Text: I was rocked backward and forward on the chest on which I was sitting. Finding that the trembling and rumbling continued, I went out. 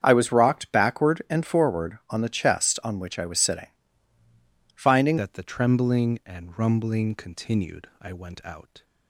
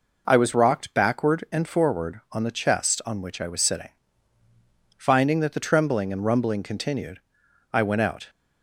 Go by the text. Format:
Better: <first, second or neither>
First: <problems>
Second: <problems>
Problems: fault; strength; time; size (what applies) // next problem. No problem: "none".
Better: second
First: starts louder than the rest; strong; until 1.0 s; 8 dB // changes voice at "that"; from 5.1 s on; 3.7 s long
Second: none